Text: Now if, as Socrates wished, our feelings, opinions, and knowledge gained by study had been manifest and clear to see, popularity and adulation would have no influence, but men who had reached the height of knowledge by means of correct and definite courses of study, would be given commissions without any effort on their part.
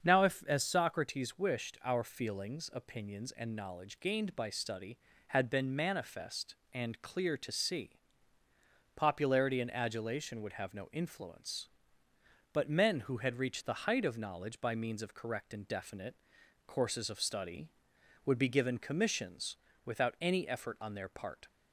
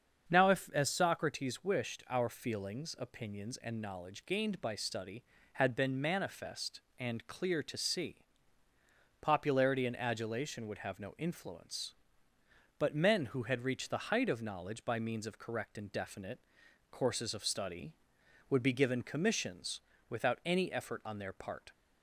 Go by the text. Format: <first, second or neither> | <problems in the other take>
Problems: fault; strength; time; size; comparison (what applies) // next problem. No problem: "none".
neither | starts louder than the rest; the same in both // pauses between "definite" and "courses"; noticeable; the same in both // pauses between "commissions" and "without"; slight; the same in both